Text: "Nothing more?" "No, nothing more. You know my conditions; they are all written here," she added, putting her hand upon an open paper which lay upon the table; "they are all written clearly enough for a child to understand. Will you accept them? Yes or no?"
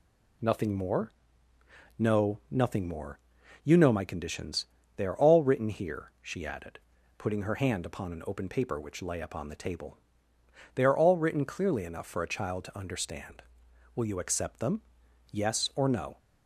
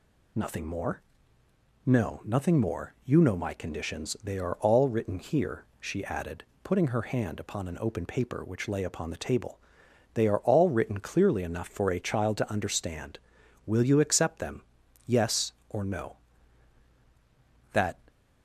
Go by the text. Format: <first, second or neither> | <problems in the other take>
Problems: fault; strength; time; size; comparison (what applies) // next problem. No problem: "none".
first | goes on to say "That"; slight; from 17.7 s on; 0.26 s long